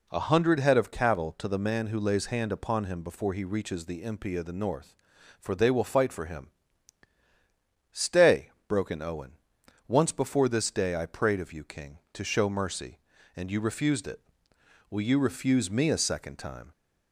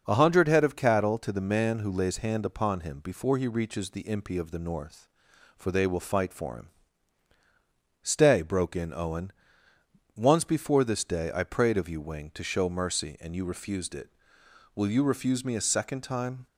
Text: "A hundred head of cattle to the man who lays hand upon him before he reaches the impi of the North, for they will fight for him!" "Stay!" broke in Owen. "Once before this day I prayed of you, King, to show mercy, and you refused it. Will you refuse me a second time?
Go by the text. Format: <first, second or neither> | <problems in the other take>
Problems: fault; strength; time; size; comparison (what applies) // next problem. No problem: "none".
first | starts louder than the rest; until 1.0 s; 6 dB // says "Wing" for "King"; at 11.9 s